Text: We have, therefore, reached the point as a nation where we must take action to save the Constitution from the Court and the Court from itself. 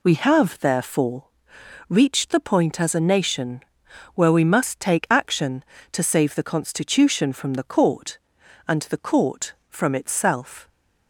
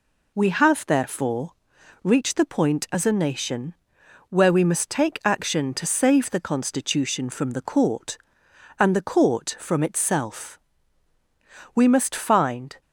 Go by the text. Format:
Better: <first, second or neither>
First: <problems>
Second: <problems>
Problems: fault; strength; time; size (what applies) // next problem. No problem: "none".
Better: first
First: pauses between "nation" and "where"; noticeable; at 3.6 s; 0.54 s long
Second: pauses between "nation" and "where"; noticeable; at 3.7 s; 0.54 s long // goes on to say "We must find"; noticeable; from 11.7 s on; 1.0 s long